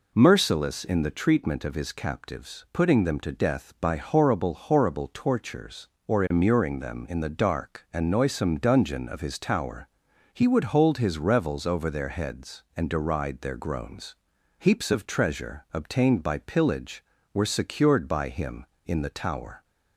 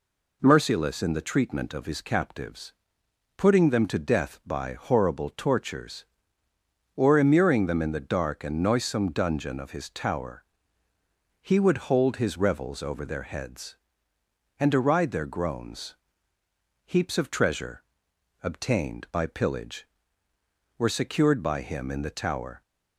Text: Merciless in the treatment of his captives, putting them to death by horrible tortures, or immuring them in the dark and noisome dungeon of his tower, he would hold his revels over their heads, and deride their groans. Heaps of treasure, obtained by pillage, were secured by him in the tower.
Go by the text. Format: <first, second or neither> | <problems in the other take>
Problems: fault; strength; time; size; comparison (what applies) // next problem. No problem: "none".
second | says "horrible" twice; at 4.5 s